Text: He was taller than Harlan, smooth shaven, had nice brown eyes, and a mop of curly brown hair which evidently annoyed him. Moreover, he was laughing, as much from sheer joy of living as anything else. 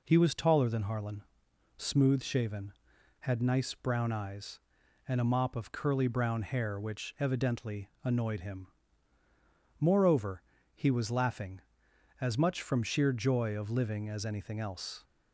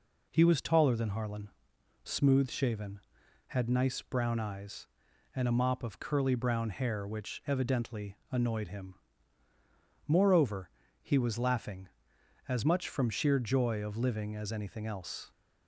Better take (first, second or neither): neither